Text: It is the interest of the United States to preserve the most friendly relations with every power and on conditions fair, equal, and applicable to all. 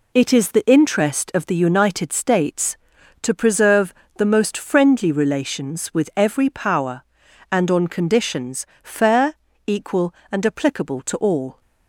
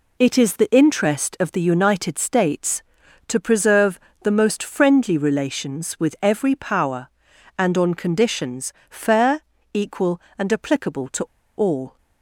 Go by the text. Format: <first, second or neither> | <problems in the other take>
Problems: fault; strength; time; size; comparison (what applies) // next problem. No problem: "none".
first | pauses between "preserve" and "the"; slight; at 3.9 s; 0.24 s long; slight in the first // pauses between "conditions" and "fair"; slight; at 8.7 s; 0.16 s long; slight in the first // pauses between "to" and "all"; slight; at 11.2 s; 0.34 s long